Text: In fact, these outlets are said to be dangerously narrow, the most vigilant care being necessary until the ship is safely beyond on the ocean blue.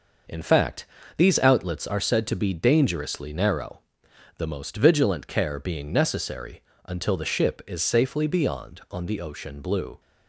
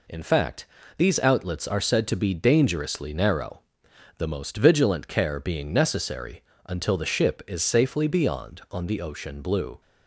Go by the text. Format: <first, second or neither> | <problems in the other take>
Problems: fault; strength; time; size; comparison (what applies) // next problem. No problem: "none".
second | starts louder than the rest; noticeable; until 1.8 s; 6 dB // pauses between "necessary" and "until"; slight; at 6.6 s; 0.24 s long; slight in the second